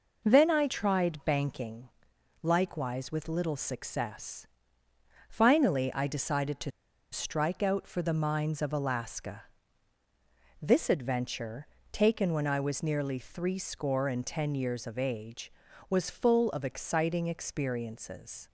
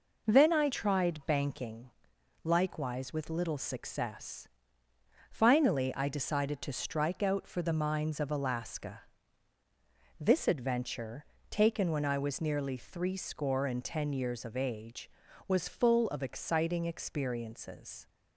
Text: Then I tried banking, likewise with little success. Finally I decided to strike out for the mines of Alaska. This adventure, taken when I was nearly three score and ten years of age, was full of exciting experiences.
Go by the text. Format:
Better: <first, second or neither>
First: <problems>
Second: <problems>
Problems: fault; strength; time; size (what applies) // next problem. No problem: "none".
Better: second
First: pauses between "to" and "strike"; at 6.7 s; 0.41 s long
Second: none